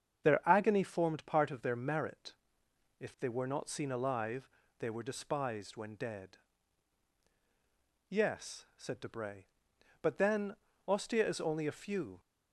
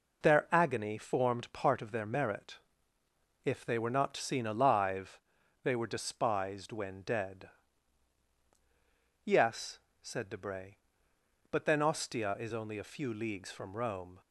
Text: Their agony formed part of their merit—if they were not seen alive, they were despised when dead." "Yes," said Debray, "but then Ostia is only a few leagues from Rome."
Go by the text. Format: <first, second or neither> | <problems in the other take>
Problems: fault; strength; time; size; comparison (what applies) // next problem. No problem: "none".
second | starts louder than the rest; strong; until 1.2 s; 7.5 dB // pauses between "then" and "Ostia"; slight; at 10.5 s; 0.30 s long // stops before "leagues from Rome"; at 12.1 s